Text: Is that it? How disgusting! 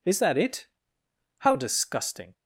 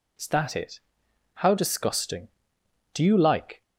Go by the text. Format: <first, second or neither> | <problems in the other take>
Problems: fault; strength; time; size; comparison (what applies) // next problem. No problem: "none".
first | goes on to say "Do you like"; noticeable; from 2.9 s on; 0.68 s long